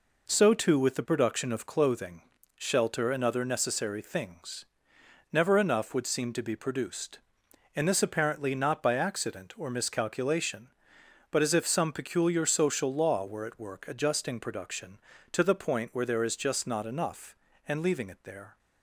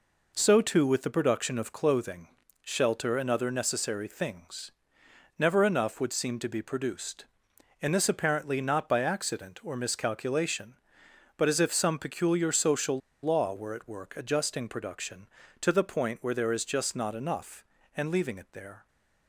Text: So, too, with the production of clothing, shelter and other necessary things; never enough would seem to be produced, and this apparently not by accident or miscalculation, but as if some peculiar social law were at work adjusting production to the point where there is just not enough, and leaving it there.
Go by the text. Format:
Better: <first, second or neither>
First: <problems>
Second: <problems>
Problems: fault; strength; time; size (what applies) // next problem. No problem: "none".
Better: first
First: none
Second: pauses between "social" and "law"; slight; at 12.9 s; 0.24 s long